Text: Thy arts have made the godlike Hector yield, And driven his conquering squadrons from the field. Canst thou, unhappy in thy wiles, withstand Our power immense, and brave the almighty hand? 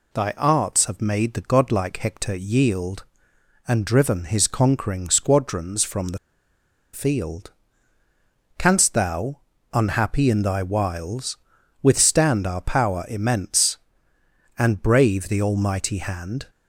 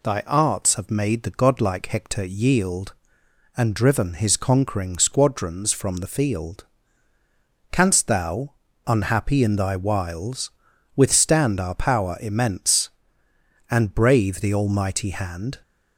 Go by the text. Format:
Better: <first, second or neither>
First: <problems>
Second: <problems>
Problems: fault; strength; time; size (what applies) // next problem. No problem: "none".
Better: second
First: pauses between "the" and "field"; noticeable; at 6.1 s; 0.76 s long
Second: none